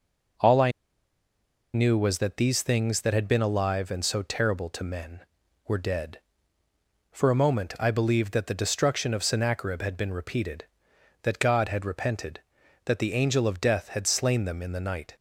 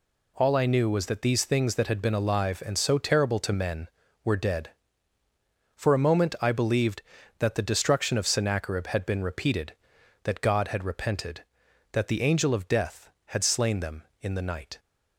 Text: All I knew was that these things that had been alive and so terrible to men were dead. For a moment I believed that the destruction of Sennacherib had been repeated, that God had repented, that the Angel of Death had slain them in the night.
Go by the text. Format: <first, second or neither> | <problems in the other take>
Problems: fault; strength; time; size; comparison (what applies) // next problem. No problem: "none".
second | pauses between "I" and "knew"; at 0.7 s; 1.0 s long